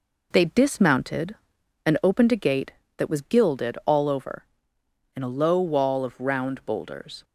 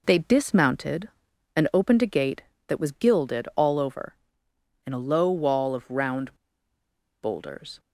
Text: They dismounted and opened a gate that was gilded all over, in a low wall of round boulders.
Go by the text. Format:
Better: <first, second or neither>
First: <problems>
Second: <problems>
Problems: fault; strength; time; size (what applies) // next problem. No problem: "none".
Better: first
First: none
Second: pauses between "round" and "boulders"; noticeable; at 6.3 s; 0.86 s long